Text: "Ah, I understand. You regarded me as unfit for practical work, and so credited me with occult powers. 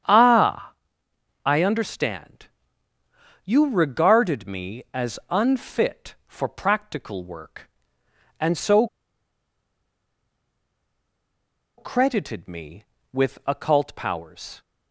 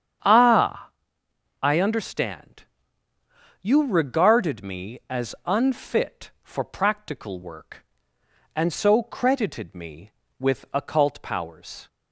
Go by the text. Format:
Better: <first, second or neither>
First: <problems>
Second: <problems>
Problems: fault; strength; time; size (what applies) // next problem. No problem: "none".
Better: second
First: starts louder than the rest; strong; until 1.7 s; 8.5 dB // pauses between "so" and "credited"; strong; at 8.8 s; 2.9 s long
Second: starts louder than the rest; strong; until 1.9 s; 8.5 dB